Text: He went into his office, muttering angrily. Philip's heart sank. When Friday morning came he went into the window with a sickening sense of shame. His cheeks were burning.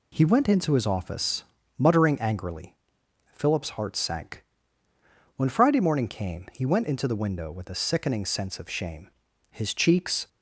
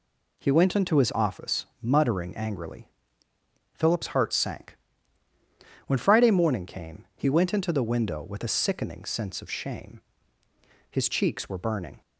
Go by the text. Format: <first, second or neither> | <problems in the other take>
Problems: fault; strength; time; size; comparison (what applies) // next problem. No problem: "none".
second | stops before "were burning"; at 10.2 s